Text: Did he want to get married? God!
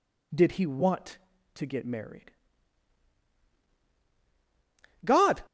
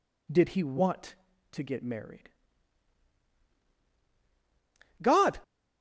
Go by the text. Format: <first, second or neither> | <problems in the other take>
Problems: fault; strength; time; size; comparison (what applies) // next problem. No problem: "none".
neither | none